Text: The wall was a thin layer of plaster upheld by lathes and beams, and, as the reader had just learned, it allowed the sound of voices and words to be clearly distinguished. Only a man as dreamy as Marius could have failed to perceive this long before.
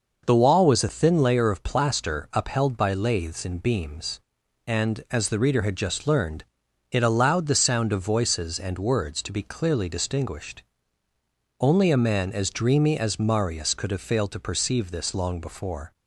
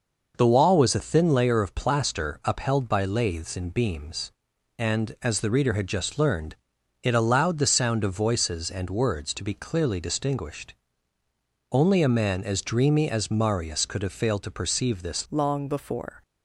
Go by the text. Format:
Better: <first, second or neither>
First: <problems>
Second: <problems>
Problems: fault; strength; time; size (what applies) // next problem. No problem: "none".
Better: first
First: none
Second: changes voice at "long"; from 15.2 s on; 1.0 s long